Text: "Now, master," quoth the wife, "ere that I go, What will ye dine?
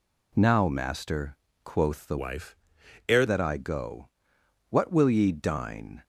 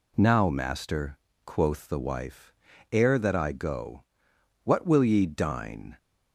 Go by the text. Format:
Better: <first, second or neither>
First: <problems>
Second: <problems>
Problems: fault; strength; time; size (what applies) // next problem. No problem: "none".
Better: second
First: changes voice from "wife" to "ere"; from 2.1 to 3.2 s; 1.1 s long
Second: none